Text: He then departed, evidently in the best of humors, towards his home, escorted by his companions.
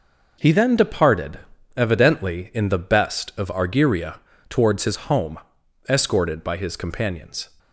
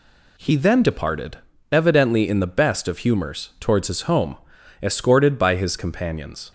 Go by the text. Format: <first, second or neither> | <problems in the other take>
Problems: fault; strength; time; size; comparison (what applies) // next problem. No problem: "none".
second | says "argyria" for "humors"; at 3.4 s